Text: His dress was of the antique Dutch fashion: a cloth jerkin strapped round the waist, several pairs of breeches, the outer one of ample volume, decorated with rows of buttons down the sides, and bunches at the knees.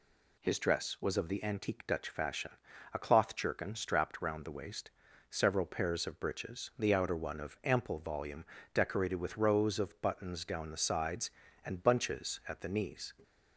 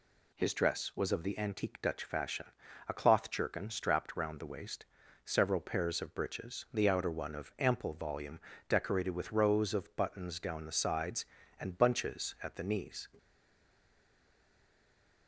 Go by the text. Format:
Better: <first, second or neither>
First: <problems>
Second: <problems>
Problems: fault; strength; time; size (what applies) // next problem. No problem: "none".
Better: first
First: none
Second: stays silent after the last word; noticeable; from 13.1 s on; 2.1 s long